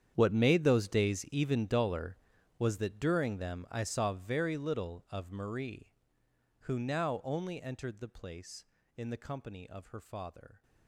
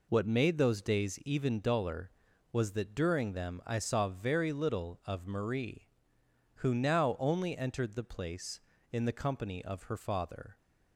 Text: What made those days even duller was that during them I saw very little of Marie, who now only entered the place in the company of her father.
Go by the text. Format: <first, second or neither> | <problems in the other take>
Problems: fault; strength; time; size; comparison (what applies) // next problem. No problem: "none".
second | gets quieter; strong; throughout; 16.5 dB